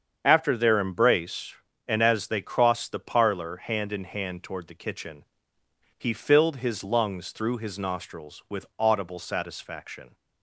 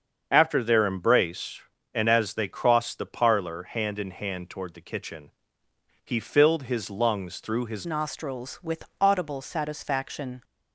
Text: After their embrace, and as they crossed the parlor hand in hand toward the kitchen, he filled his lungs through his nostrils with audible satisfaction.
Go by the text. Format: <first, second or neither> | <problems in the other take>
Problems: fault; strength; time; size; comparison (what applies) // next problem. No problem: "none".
first | starts louder than the rest; until 1.3 s; 7 dB; strong in the first // changes voice at "nostrils"; from 7.8 s on; 2.6 s long // pauses between "with" and "audible"; slight; at 8.8 s; 0.18 s long